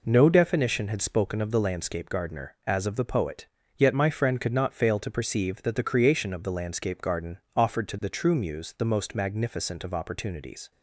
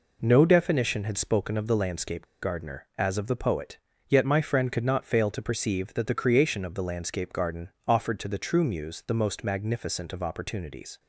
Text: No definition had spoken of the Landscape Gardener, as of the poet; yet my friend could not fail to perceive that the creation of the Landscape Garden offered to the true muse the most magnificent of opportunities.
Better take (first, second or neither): first